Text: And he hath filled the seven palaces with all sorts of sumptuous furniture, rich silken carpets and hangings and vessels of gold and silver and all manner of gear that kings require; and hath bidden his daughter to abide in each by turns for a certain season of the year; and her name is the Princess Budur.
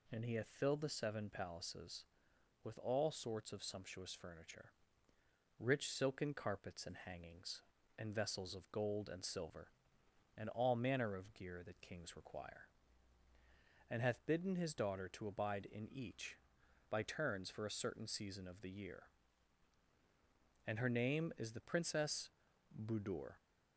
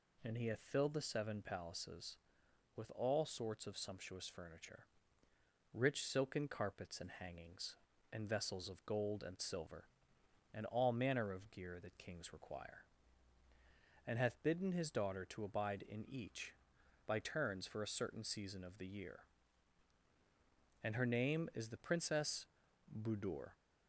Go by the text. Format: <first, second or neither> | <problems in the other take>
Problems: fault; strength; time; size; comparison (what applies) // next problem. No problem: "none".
neither | pauses between "Princess" and "Budur"; noticeable; the same in both